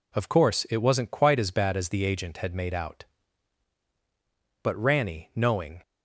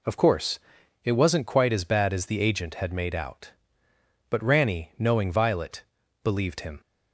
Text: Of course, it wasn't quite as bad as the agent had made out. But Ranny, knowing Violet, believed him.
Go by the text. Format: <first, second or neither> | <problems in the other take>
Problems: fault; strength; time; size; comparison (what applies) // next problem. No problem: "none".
second | stops before "Violet believed him"; at 5.8 s